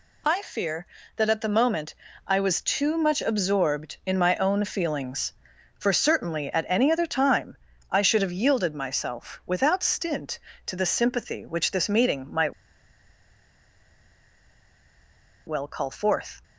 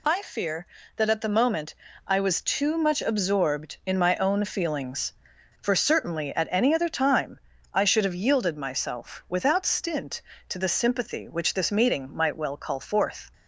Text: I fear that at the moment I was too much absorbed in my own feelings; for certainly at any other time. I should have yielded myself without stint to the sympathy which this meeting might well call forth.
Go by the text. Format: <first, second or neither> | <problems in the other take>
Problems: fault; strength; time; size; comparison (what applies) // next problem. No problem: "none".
second | pauses between "moment" and "I"; slight; at 1.9 s; 0.32 s long; slight in the second // pauses between "might" and "well"; strong; at 12.5 s; 2.9 s long